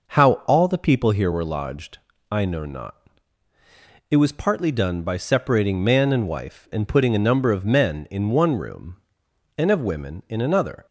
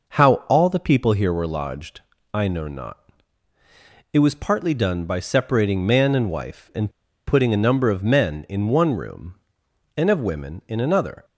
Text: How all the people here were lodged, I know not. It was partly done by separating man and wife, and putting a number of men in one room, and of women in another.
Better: first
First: none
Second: pauses between "and" and "putting"; at 6.8 s; 0.38 s long

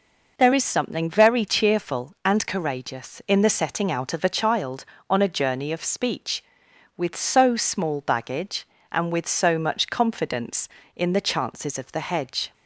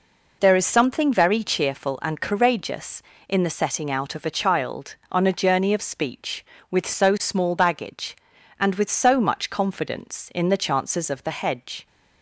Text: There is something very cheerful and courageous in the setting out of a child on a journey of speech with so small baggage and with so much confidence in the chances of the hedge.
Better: neither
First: none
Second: none

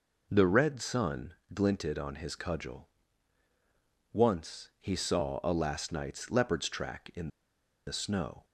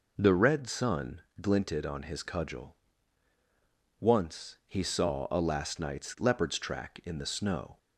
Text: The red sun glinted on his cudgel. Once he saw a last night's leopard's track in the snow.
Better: second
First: pauses between "sun" and "glinted"; slight; at 1.3 s; 0.22 s long // pauses between "in" and "the"; noticeable; at 7.2 s; 0.56 s long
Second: pauses between "sun" and "glinted"; slight; at 1.1 s; 0.22 s long

